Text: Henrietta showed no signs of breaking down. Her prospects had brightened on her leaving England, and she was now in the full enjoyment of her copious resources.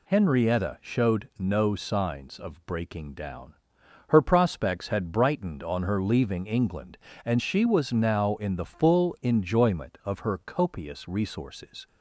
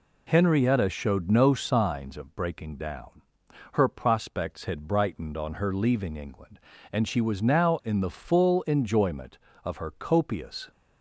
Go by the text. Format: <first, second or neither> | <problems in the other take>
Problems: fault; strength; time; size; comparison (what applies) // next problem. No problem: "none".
first | stops before "resources"; at 10.7 s